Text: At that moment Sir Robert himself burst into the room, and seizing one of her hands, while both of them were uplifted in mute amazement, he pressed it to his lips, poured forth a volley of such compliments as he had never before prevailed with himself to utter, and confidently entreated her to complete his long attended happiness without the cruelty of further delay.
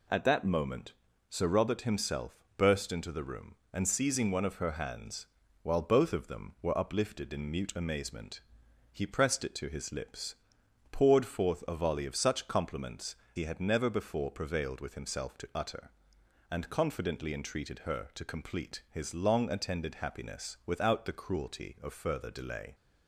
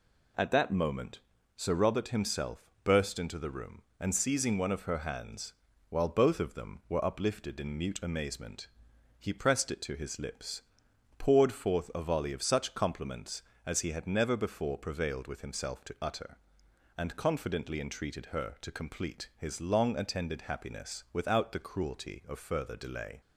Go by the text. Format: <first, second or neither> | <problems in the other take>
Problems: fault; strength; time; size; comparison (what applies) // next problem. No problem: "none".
second | pauses between "moment" and "Sir"; slight; at 0.9 s; 0.36 s long; slight in the second // pauses between "himself" and "burst"; slight; at 2.3 s; 0.18 s long; slight in the second // skips "as"; at 13.2 s